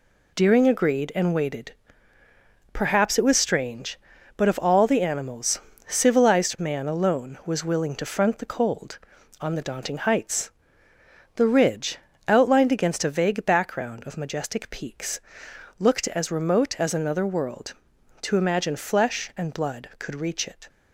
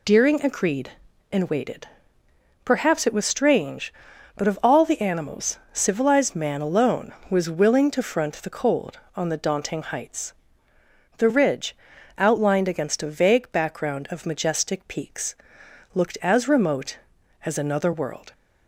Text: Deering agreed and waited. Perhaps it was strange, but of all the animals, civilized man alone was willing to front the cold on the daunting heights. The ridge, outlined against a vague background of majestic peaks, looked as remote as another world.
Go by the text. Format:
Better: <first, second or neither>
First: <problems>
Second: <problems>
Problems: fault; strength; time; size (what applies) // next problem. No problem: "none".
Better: second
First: goes on to say "To imagine flesh and blood could reach it"; strong; from 18.2 s on; 2.4 s long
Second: none